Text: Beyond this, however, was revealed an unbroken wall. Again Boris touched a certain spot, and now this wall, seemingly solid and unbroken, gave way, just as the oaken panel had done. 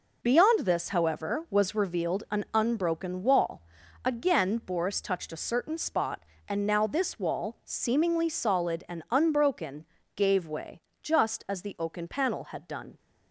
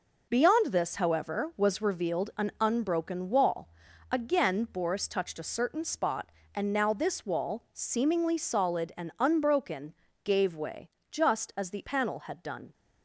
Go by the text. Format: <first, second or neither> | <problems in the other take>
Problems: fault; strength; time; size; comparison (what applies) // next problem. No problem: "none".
first | skips "oaken"; at 11.8 s